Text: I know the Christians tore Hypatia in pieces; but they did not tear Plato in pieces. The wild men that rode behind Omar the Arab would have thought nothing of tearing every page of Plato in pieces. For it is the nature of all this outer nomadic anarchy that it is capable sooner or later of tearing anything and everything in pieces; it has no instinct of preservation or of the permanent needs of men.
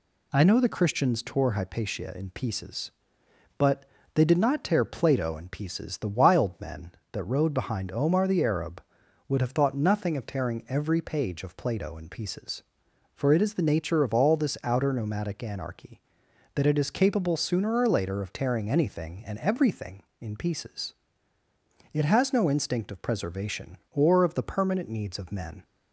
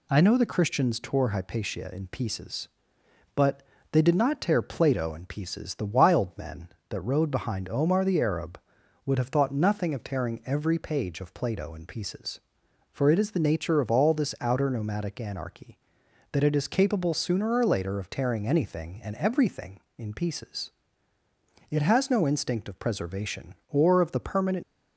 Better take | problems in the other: first | pauses between "but" and "they"; slight; at 3.6 s; 0.30 s long; slight in the first // stops before "needs of men"; at 24.6 s

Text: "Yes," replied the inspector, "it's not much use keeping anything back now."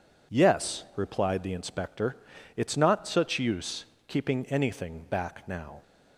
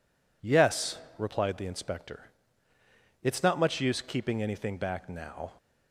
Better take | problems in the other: second | says "such" for "much"; at 3.0 s // pauses between "use" and "keeping"; slight; at 3.8 s; 0.20 s long

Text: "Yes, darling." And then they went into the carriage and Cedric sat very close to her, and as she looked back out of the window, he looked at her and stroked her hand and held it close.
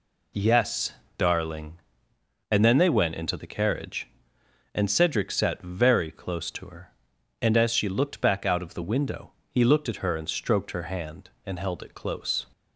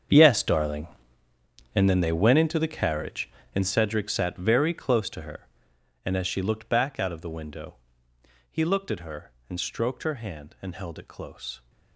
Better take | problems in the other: first | gets quieter; strong; throughout; 15 dB

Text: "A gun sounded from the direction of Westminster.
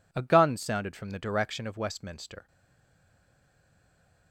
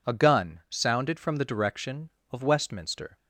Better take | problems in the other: second | stays silent after the last word; noticeable; from 2.4 s on; 1.9 s long

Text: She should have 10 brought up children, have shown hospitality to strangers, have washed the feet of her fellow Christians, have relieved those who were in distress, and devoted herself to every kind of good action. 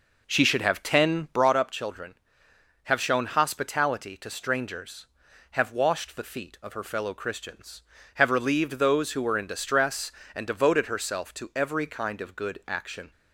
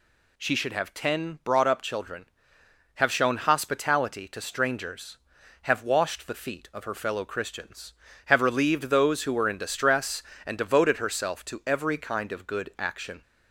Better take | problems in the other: second | starts louder than the rest; noticeable; until 1.6 s; 4.5 dB

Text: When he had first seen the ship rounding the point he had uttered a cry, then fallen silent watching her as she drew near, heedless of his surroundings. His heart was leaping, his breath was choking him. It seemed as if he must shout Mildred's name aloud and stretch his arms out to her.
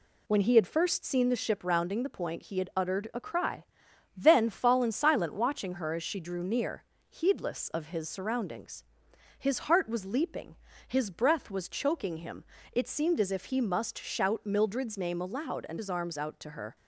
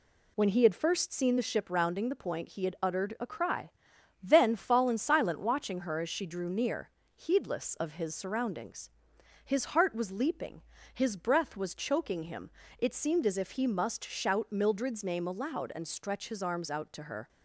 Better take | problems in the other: second | skips "stretch"; at 15.7 s

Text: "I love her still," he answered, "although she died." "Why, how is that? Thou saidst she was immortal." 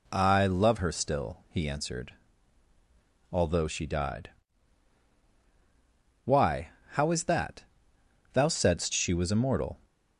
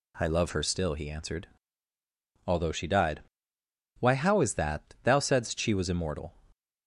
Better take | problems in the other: neither | none

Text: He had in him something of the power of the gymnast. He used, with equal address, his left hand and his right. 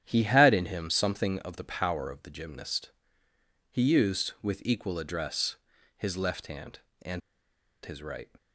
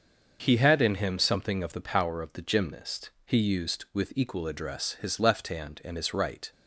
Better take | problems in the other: second | starts louder than the rest; strong; until 1.0 s; 9.5 dB; also in the second // pauses between "and" and "his"; noticeable; at 7.2 s; 0.65 s long

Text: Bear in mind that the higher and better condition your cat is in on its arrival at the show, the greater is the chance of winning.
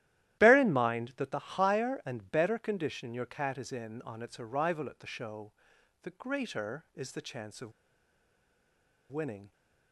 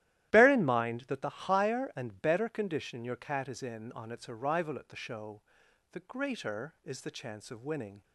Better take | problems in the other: second | starts louder than the rest; strong; until 1.4 s; 13.5 dB; strong in the second // pauses between "of" and "winning"; strong; at 7.7 s; 1.3 s long

